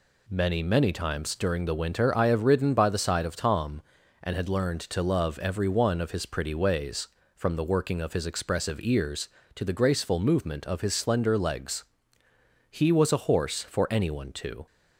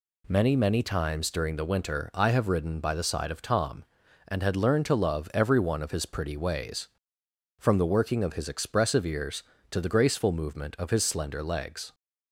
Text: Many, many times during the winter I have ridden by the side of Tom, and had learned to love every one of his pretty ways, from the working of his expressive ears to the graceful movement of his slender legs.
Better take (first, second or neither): second